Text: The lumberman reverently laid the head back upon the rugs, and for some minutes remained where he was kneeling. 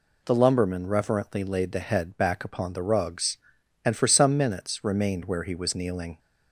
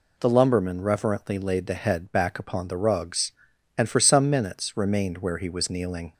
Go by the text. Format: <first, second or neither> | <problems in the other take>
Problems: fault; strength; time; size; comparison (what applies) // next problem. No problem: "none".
neither | none